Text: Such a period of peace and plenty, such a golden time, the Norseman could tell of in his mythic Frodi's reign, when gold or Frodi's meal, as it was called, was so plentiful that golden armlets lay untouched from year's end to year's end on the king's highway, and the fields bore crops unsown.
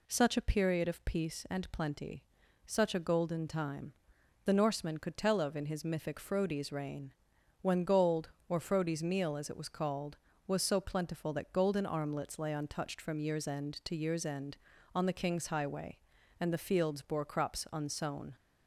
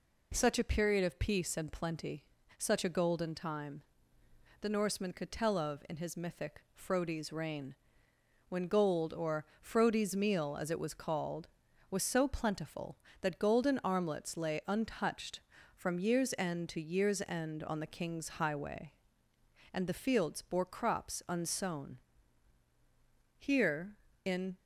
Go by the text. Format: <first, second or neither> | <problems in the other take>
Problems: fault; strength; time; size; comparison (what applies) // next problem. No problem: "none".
first | pauses between "or" and "Frodi's"; slight; at 9.4 s; 0.16 s long // goes on to say "Here in"; noticeable; from 23.3 s on; 1.2 s long